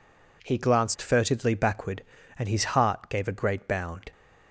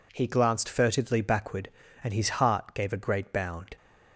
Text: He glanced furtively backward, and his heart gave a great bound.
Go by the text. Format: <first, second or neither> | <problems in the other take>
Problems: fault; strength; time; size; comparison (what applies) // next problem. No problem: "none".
neither | none